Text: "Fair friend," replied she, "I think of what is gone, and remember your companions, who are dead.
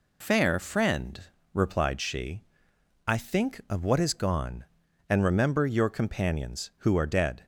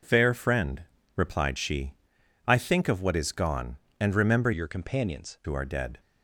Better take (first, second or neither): first